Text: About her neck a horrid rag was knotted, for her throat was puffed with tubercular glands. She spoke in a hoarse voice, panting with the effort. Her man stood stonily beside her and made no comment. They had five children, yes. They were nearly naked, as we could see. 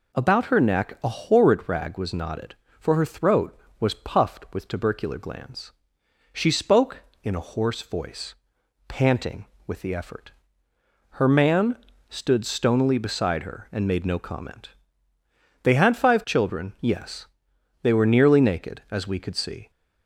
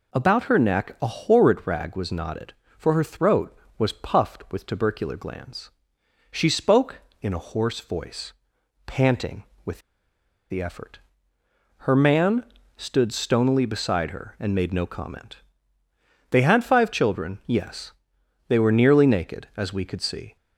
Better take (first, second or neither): first